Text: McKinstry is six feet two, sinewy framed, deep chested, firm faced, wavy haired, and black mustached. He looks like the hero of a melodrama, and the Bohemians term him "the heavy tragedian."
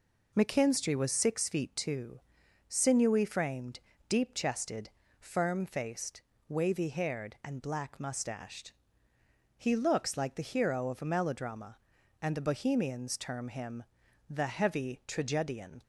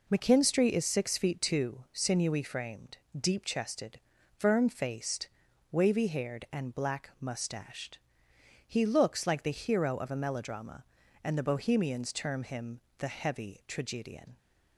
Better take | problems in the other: second | says "was" for "is"; at 0.9 s // pauses between "him" and "the"; at 13.8 s; 0.44 s long; slight in the second

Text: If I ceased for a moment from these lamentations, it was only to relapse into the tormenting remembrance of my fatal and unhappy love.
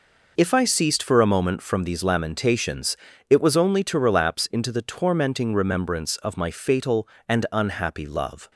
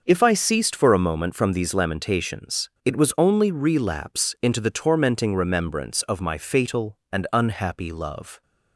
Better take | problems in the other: first | skips "to"; at 3.5 s

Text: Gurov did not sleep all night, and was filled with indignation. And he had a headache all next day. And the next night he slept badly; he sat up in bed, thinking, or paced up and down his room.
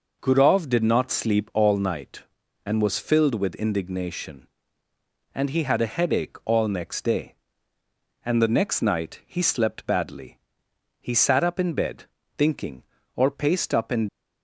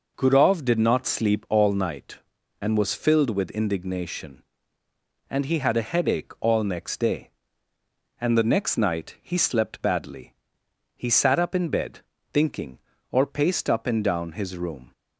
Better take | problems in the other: second | stops before "down his room"; at 14.0 s

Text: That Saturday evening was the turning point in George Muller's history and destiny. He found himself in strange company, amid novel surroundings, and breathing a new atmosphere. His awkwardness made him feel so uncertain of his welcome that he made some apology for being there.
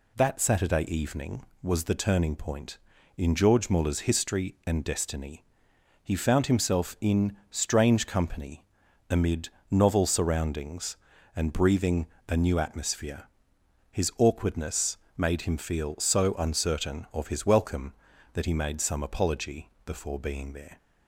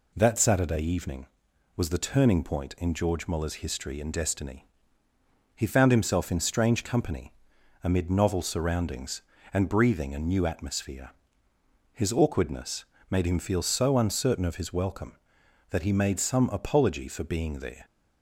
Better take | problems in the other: second | pauses between "amid" and "novel"; slight; at 9.4 s; 0.24 s long // pauses between "breathing" and "a"; slight; at 12.0 s; 0.22 s long // pauses between "awkwardness" and "made"; slight; at 14.9 s; 0.20 s long; slight in the second // says "before" for "for"; at 19.8 s

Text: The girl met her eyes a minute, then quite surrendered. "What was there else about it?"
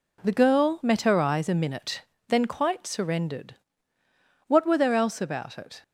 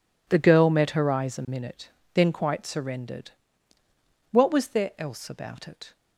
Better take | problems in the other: second | says "were" for "was"; at 4.6 s

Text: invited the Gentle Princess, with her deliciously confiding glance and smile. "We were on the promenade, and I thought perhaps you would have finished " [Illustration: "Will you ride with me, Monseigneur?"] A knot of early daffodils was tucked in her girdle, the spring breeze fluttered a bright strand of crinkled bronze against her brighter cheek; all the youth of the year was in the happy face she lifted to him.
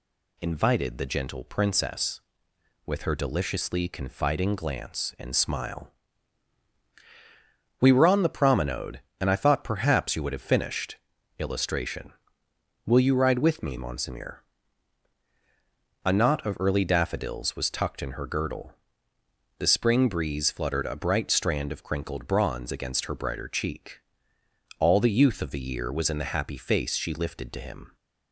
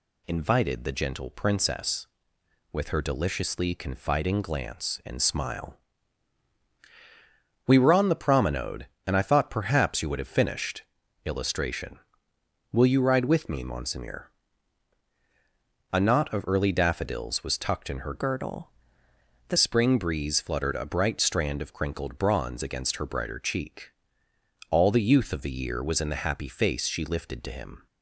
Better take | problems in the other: first | changes voice from "girdle" to "the"; from 18.1 to 19.5 s; 1.4 s long

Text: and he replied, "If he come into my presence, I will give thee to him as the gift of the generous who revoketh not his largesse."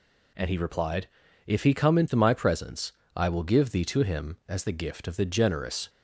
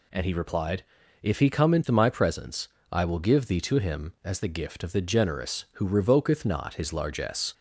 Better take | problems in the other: second | stops before "who revoketh not his largesse"; at 5.8 s

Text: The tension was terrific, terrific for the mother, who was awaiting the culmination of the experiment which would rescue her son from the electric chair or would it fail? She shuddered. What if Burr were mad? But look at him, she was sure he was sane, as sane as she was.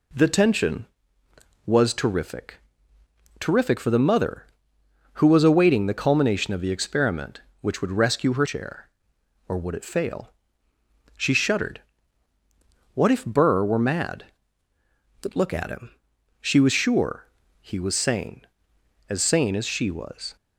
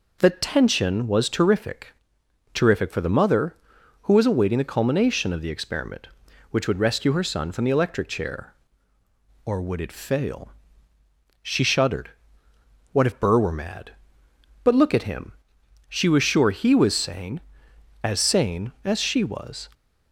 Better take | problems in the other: second | skips "son from the electric"; at 8.4 s // pauses between "sure" and "he"; slight; at 17.2 s; 0.34 s long

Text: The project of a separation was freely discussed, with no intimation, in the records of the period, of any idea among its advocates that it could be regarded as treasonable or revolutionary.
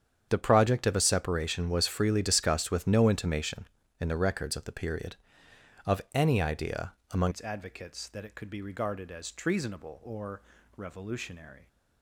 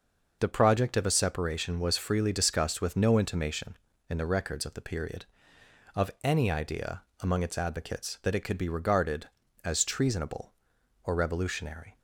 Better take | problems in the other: second | starts louder than the rest; strong; until 1.3 s; 8.5 dB // pauses between "idea" and "among"; slight; at 6.9 s; 0.18 s long; slight in the second // changes voice at "its"; from 7.3 s on; 4.3 s long // pauses between "or" and "revolutionary"; slight; at 10.4 s; 0.34 s long

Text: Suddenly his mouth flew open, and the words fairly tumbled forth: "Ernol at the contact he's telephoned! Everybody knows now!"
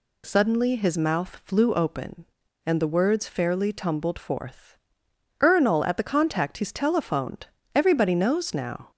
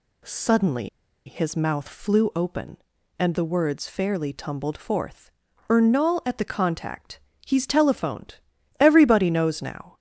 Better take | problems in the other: first | pauses between "Suddenly" and "his"; at 0.8 s; 0.38 s long // pauses between "contact" and "he's"; slight; at 7.1 s; 0.28 s long

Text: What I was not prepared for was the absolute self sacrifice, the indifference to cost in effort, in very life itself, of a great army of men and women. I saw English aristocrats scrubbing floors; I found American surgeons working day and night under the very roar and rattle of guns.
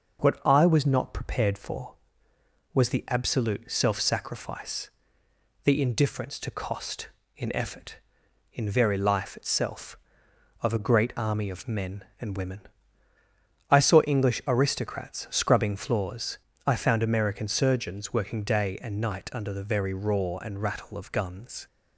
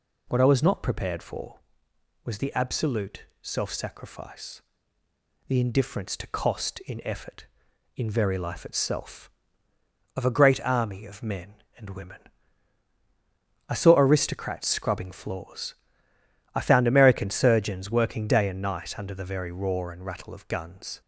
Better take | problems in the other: first | pauses between "absolute" and "self"; slight; at 3.2 s; 0.16 s long // skips "English"; at 13.9 s

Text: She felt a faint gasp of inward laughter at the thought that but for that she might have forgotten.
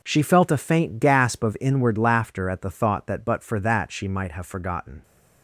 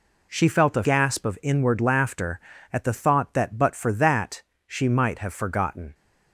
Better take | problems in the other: first | skips "faint"; at 0.8 s // pauses between "that" and "she"; slight; at 4.4 s; 0.24 s long

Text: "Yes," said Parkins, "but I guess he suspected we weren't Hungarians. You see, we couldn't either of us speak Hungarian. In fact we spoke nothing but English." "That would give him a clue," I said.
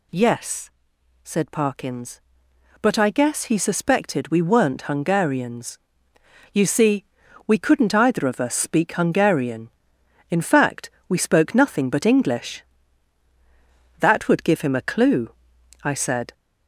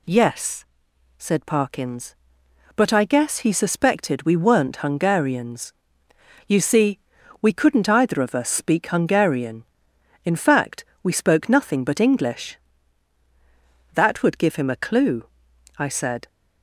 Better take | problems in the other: second | gets louder; slight; throughout; 3.5 dB // pauses between "fact" and "we"; slight; at 10.8 s; 0.20 s long; slight in the second

